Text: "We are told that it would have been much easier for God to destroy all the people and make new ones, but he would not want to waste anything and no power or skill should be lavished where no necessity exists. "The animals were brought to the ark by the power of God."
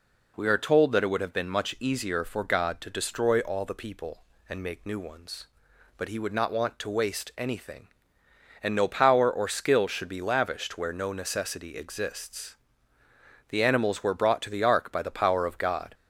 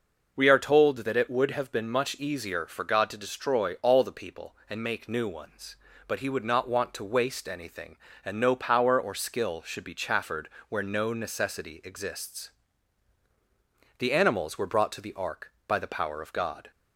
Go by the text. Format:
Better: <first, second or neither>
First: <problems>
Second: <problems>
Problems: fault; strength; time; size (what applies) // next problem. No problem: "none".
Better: first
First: none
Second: says "chaffered" for "lavished"; at 9.9 s